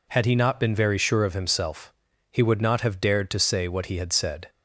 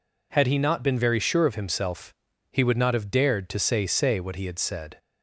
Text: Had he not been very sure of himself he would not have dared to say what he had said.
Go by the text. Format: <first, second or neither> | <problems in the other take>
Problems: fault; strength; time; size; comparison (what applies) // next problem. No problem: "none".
first | pauses between "himself" and "he"; at 2.1 s; 0.38 s long; also in the first // says "say" twice; at 3.8 s